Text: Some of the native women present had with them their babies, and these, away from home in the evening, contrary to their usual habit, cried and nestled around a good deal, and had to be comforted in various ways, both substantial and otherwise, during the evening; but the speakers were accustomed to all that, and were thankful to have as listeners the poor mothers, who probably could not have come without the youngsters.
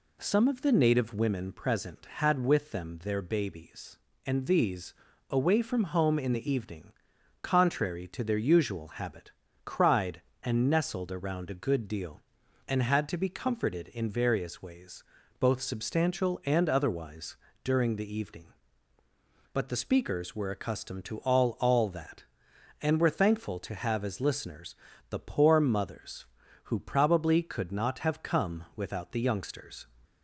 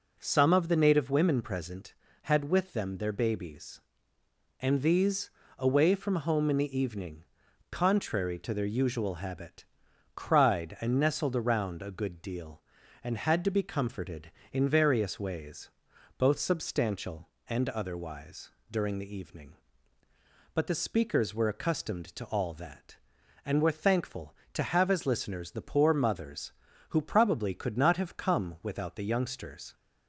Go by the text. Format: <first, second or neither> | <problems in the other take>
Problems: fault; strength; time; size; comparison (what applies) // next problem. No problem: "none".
second | says "all" twice; at 21.6 s // pauses between "listeners" and "the"; slight; at 24.7 s; 0.36 s long